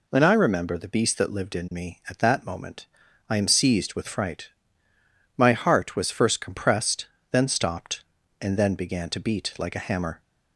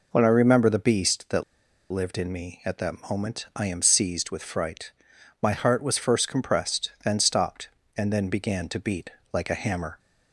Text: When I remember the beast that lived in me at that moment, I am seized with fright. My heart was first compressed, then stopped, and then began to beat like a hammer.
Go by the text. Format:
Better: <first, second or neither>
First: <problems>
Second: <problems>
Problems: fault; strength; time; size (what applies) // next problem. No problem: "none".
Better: first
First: none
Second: pauses between "that" and "lived"; noticeable; at 1.4 s; 0.48 s long // pauses between "beat" and "like"; slight; at 9.1 s; 0.22 s long